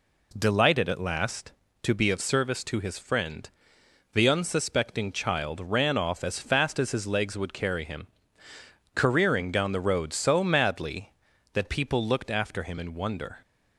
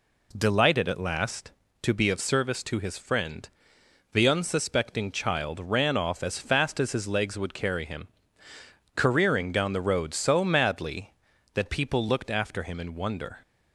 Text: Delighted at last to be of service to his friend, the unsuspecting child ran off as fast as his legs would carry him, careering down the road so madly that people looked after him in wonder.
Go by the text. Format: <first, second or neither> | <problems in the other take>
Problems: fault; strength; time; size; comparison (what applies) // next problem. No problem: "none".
neither | none